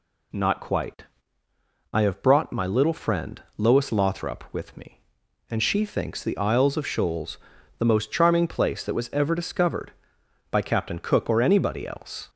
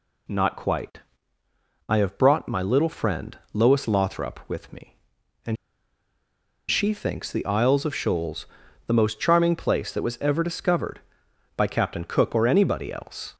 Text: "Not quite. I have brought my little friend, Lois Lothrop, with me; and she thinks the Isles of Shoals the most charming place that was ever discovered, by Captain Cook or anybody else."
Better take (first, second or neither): first